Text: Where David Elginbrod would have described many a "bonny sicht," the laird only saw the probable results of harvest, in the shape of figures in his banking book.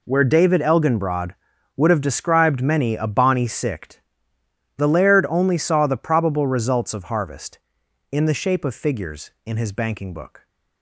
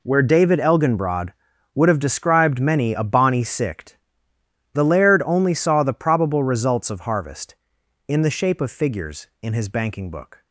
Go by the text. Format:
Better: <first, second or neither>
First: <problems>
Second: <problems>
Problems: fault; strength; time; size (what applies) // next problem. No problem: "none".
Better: neither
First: none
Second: none